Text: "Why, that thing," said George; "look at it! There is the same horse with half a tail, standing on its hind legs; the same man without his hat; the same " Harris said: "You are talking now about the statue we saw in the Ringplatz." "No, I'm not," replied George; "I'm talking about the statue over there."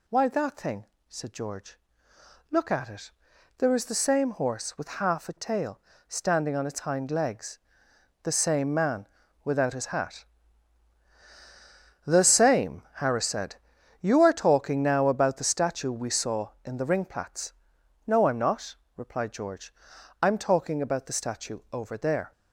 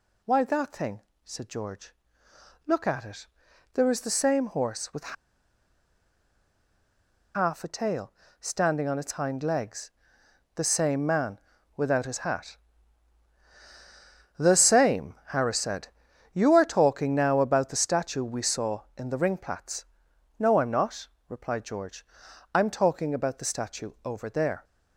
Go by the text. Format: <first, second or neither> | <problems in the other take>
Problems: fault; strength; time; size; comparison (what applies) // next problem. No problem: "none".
first | pauses between "with" and "half"; strong; at 5.1 s; 2.2 s long // pauses between "man" and "without"; at 11.3 s; 0.38 s long; also in the first